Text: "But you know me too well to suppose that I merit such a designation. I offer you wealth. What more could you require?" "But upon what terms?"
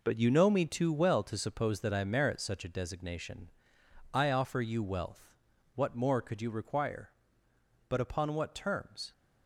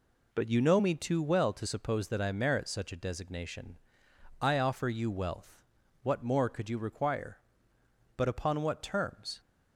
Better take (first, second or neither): second